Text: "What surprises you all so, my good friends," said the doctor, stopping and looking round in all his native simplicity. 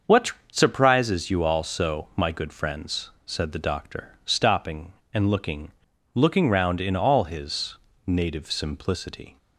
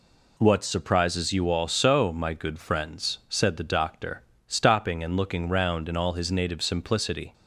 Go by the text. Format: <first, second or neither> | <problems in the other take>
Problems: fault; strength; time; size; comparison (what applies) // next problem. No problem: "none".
second | starts louder than the rest; until 1.2 s; 6.5 dB // pauses between "What" and "surprises"; slight; at 0.3 s; 0.18 s long // says "looking" twice; at 6.1 s // pauses between "his" and "native"; slight; at 7.7 s; 0.28 s long